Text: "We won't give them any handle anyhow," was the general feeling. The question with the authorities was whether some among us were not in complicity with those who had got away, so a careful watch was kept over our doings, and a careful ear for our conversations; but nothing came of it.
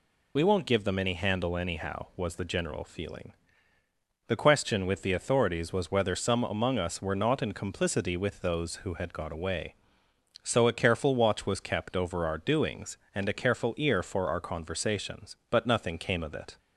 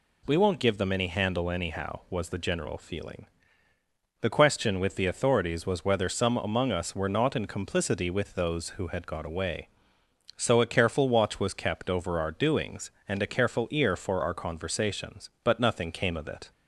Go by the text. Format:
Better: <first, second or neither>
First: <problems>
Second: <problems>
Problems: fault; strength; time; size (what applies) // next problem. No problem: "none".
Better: second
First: loses the start of "We"; at 0.3 s; 35 ms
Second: none